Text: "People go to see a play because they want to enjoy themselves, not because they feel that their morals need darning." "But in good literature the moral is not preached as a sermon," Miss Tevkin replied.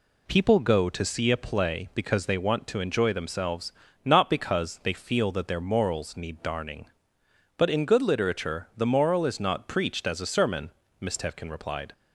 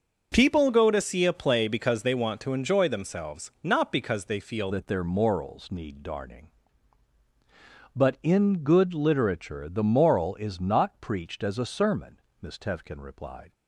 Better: first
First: none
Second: starts louder than the rest; noticeable; until 1.3 s; 6 dB // changes voice at "that"; from 4.7 s on; 8.8 s long

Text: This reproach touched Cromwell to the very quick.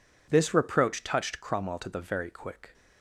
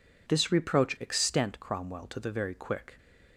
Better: first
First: none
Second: says "extent" for "touched"; at 1.0 s

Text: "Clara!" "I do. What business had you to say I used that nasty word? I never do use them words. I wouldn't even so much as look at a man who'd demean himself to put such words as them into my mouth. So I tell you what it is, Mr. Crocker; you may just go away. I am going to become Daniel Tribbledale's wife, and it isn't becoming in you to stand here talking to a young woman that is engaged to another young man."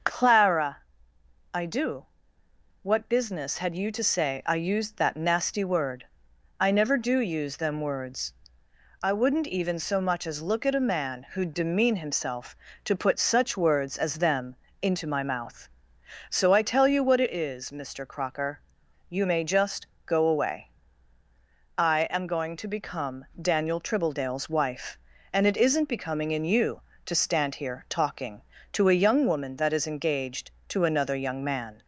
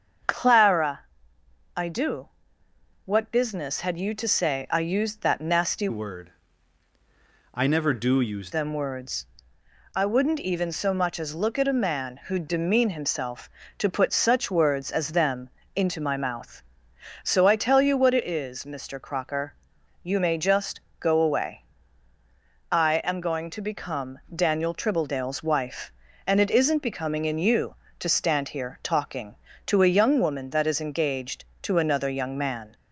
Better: first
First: starts louder than the rest; noticeable; until 1.7 s; 6 dB // pauses between "them" and "into"; slight; at 14.5 s; 0.26 s long // pauses between "just" and "go"; slight; at 19.8 s; 0.18 s long // pauses between "become" and "Daniel"; slight; at 23.2 s; 0.16 s long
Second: starts louder than the rest; until 2.0 s; 7 dB // changes voice from "word" to "use"; from 5.8 to 8.5 s; 2.7 s long // pauses between "them" and "into"; slight; at 15.5 s; 0.26 s long // pauses between "just" and "go"; slight; at 20.8 s; 0.18 s long // pauses between "become" and "Daniel"; slight; at 24.1 s; 0.16 s long

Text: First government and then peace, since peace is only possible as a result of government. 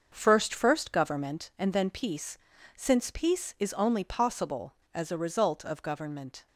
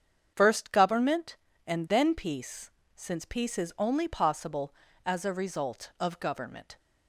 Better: second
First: starts louder than the rest; until 1.1 s; 6.5 dB // says "First" twice; at 0.5 s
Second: starts louder than the rest; strong; until 1.3 s; 7.5 dB

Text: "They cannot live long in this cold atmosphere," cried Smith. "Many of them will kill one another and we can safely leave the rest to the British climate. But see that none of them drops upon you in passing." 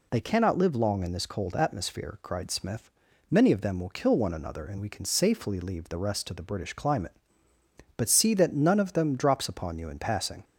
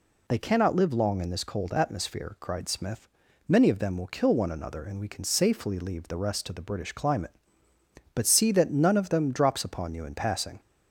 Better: neither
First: none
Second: none

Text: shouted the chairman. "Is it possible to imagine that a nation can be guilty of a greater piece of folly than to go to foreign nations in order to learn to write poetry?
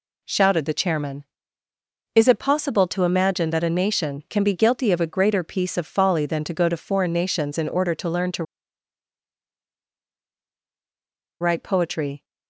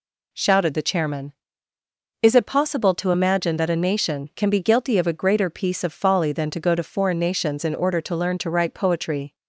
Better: second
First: pauses between "to" and "write"; strong; at 8.4 s; 2.9 s long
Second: none

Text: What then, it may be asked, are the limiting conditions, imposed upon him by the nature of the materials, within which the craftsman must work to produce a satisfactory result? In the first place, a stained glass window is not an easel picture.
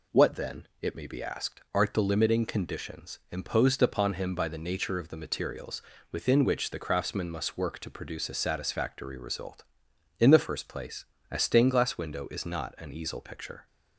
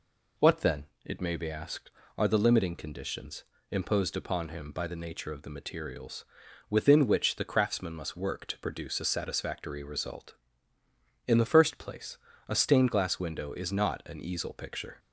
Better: second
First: says "art" for "are"; at 1.7 s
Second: none

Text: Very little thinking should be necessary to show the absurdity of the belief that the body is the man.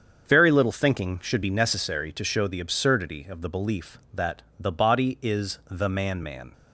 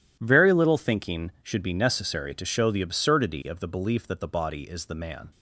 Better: second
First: starts louder than the rest; strong; until 1.3 s; 7 dB // pauses between "that" and "the"; slight; at 4.4 s; 0.16 s long // says "man" twice; at 6.2 s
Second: none

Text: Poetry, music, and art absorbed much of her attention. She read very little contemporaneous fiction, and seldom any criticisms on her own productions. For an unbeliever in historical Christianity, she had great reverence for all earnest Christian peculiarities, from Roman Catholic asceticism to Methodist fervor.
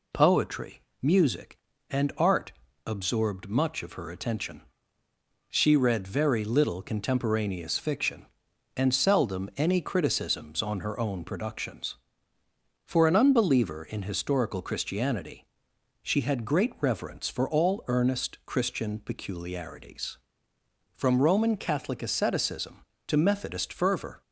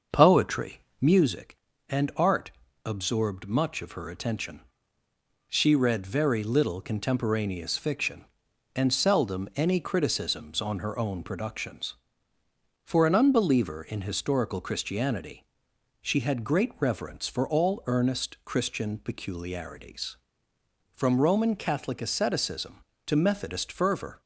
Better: first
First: pauses between "art" and "absorbed"; slight; at 2.5 s; 0.34 s long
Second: starts louder than the rest; until 1.3 s; 6.5 dB // pauses between "art" and "absorbed"; slight; at 2.5 s; 0.34 s long

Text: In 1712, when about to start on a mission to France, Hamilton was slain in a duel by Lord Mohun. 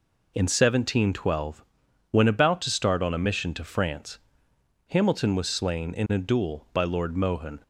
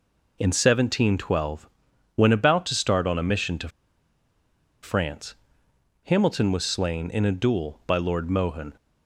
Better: first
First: none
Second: pauses between "to" and "France"; at 3.6 s; 1.1 s long

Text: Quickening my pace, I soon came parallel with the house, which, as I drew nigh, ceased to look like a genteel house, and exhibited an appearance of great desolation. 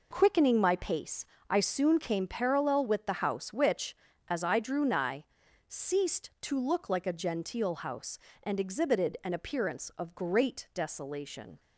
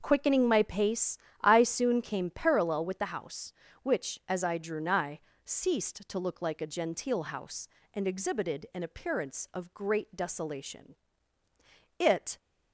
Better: first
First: none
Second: starts louder than the rest; noticeable; until 1.0 s; 6 dB // goes on to say "It"; slight; from 11.9 s on; 0.38 s long

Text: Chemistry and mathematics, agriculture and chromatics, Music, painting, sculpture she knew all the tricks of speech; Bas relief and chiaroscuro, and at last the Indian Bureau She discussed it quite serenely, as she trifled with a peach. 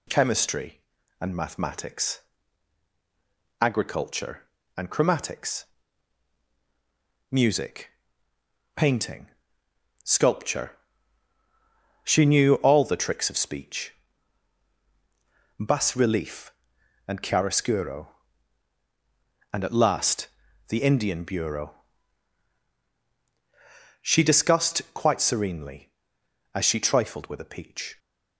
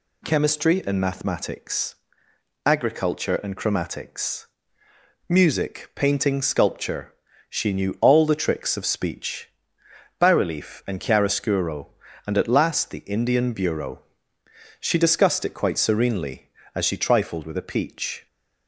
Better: second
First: pauses between "sculpture" and "she"; strong; at 10.7 s; 1.3 s long // pauses between "last" and "the"; at 20.2 s; 0.42 s long // pauses between "Bureau" and "She"; strong; at 21.7 s; 2.2 s long // skips "it"; at 24.8 s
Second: pauses between "sculpture" and "she"; slight; at 7.1 s; 0.36 s long // pauses between "Bureau" and "She"; noticeable; at 14.0 s; 0.78 s long

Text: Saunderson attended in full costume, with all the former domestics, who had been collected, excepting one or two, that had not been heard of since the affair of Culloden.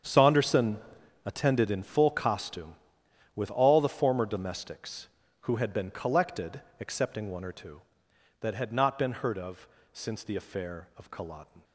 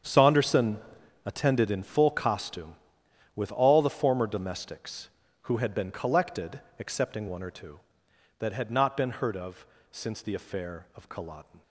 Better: neither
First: starts louder than the rest; strong; until 1.5 s; 8 dB // pauses between "Saunderson" and "attended"; noticeable; at 0.7 s; 0.48 s long // pauses between "of" and "since"; slight; at 9.6 s; 0.28 s long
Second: starts louder than the rest; strong; until 1.5 s; 8 dB // pauses between "Saunderson" and "attended"; noticeable; at 0.7 s; 0.48 s long // pauses between "of" and "since"; slight; at 9.6 s; 0.28 s long

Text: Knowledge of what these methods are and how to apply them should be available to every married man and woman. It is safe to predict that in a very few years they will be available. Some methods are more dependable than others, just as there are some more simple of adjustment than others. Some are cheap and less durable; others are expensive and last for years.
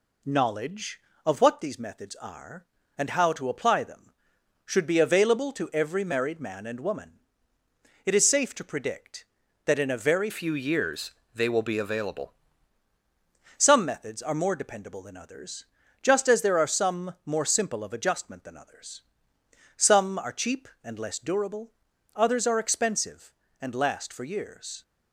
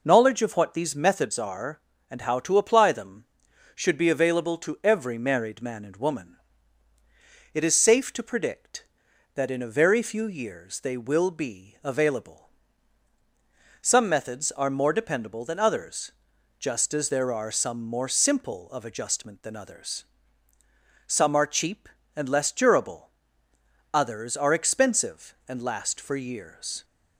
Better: second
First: changes voice from "few" to "available"; from 10.2 to 12.3 s; 2.1 s long // pauses between "years" and "they"; slight; at 11.1 s; 0.24 s long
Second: none

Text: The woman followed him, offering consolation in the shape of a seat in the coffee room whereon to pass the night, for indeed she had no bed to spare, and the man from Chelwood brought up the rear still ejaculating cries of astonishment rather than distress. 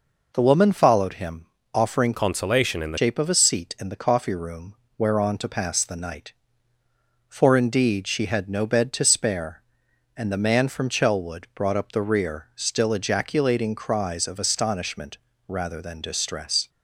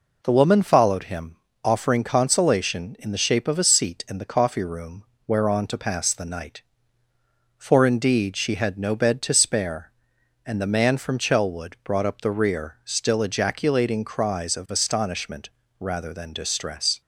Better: second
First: changes voice from "consolation" to "the"; from 2.1 to 2.9 s; 0.8 s long // pauses between "room" and "whereon"; slight; at 4.7 s; 0.22 s long // pauses between "astonishment" and "rather"; slight; at 15.1 s; 0.32 s long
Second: pauses between "room" and "whereon"; slight; at 5.0 s; 0.22 s long // pauses between "astonishment" and "rather"; slight; at 15.4 s; 0.32 s long

